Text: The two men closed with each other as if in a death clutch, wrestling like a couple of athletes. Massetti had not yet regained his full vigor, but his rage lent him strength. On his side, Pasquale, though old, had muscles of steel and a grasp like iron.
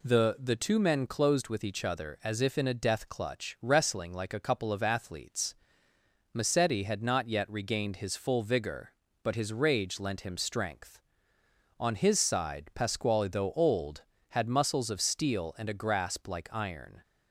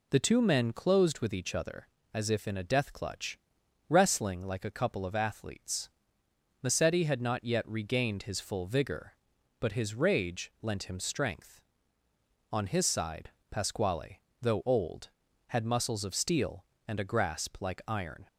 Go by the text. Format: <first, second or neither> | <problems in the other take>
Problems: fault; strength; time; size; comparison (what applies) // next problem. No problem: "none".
second | says "The" twice; at 0.3 s